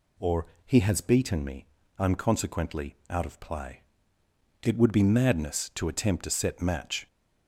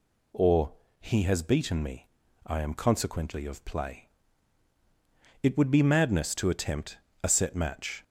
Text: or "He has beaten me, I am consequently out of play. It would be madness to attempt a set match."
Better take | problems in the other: first | pauses between "or" and "He"; slight; at 0.7 s; 0.26 s long; slight in the first // skips "out"; at 3.4 s // pauses between "attempt" and "a"; slight; at 6.9 s; 0.26 s long

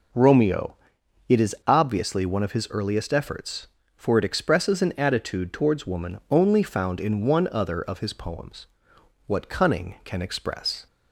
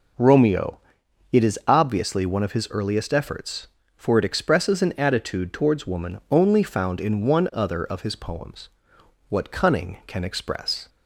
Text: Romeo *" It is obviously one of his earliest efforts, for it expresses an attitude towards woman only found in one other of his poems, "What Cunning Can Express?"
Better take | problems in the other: neither | none

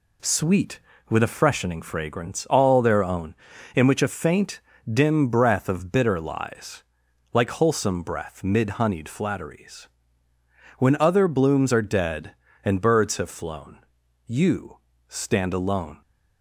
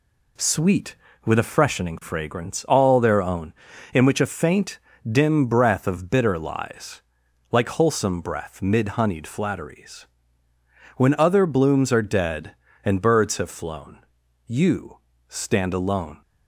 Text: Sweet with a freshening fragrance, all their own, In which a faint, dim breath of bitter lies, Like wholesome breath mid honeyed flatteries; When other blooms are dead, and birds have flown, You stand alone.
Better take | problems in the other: neither | pauses between "You" and "stand"; slight; the same in both

